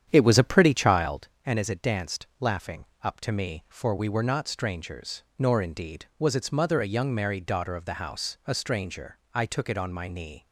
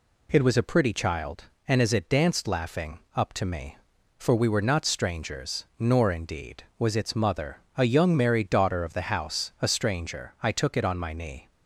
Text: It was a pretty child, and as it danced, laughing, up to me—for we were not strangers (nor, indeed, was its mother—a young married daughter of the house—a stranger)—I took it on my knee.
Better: second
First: starts louder than the rest; strong; until 1.3 s; 9 dB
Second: none

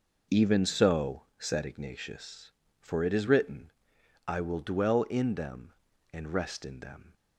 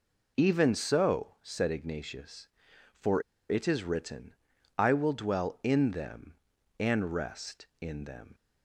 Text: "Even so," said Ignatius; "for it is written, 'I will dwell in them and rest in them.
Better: first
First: none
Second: pauses between "for" and "it"; slight; at 3.2 s; 0.28 s long

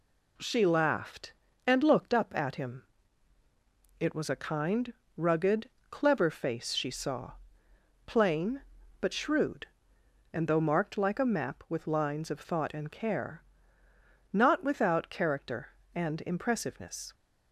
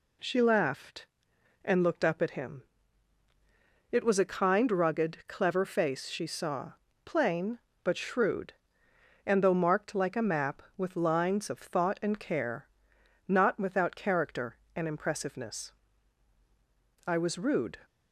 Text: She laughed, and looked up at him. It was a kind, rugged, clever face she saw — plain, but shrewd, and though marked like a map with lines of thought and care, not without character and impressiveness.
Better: first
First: none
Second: goes on to say "I was rude"; noticeable; from 17.0 s on; 0.70 s long

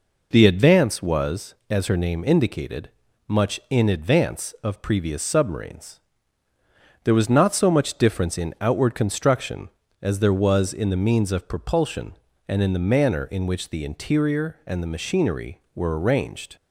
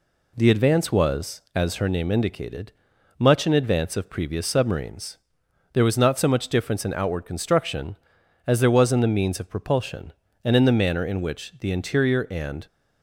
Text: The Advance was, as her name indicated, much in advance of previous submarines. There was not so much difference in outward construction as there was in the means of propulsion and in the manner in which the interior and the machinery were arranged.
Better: first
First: none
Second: stops before "the machinery were arranged"; at 12.6 s

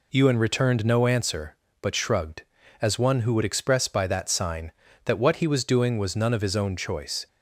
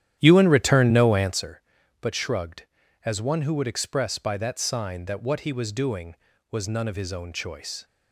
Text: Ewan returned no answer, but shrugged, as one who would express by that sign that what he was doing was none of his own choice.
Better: first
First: none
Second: starts louder than the rest; strong; until 1.4 s; 11 dB

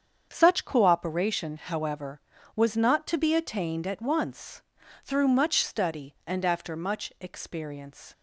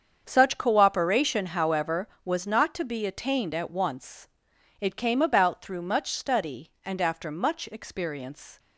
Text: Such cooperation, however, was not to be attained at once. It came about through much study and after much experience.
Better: second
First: starts louder than the rest; strong; until 1.3 s; 7.5 dB // skips "It came about"; at 4.8 s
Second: starts louder than the rest; strong; until 1.2 s; 7 dB

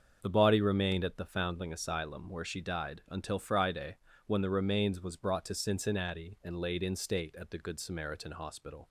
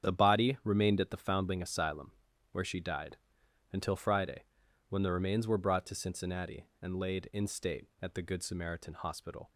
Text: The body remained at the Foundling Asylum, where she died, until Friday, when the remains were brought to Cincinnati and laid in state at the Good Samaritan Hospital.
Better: second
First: starts louder than the rest; until 1.2 s; 6.5 dB // says "was" for "were"; at 5.0 s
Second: starts louder than the rest; strong; until 1.1 s; 8 dB

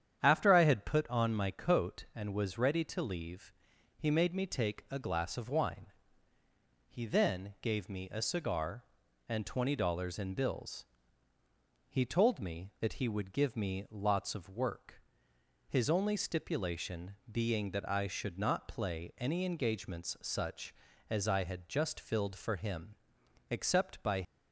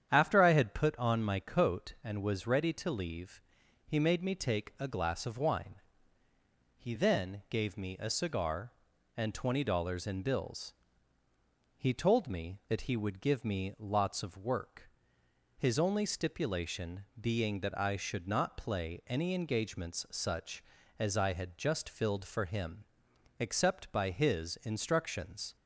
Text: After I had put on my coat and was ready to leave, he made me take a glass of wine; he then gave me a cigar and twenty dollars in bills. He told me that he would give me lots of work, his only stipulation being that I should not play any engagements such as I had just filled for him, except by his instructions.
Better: second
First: starts louder than the rest; strong; until 1.2 s; 9 dB // stops before "his instructions"; at 24.2 s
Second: starts louder than the rest; strong; until 1.1 s; 8.5 dB

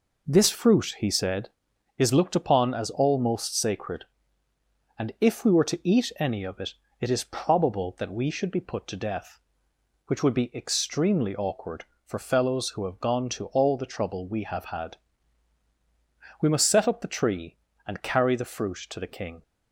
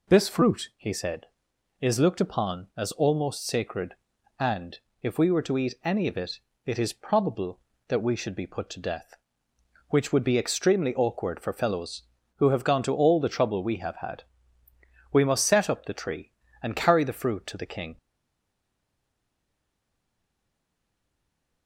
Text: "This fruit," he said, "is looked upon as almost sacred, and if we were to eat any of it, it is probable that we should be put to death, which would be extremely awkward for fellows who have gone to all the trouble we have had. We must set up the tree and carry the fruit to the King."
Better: first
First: none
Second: pauses between "and" and "if"; slight; at 4.7 s; 0.22 s long // stays silent after the last word; strong; from 17.9 s on; 3.7 s long

